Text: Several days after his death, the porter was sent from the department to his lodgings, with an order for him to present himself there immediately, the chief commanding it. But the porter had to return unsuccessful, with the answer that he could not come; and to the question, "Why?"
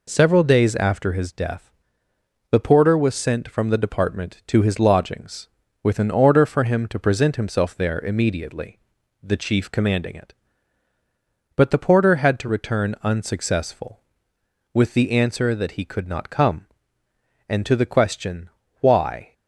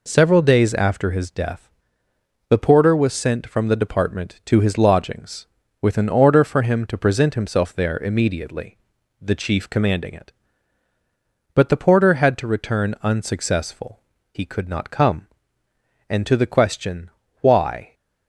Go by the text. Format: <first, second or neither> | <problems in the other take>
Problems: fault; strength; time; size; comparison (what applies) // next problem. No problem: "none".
first | skips "with the answer that"; at 14.1 s